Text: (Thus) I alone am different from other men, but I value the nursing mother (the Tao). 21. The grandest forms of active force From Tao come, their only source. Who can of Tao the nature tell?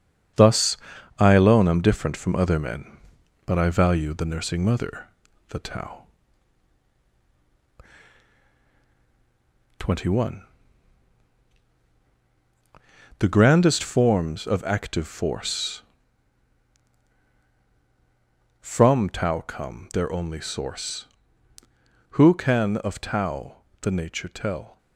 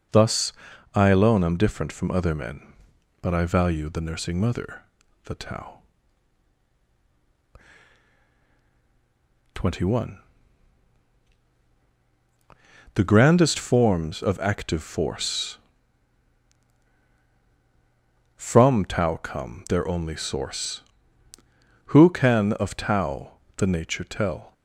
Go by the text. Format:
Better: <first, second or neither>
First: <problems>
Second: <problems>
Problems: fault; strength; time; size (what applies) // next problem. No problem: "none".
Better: second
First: gets quieter; noticeable; throughout; 6 dB // pauses between "Tao" and "the"; slight; at 23.5 s; 0.24 s long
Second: pauses between "Tao" and "the"; slight; at 23.3 s; 0.24 s long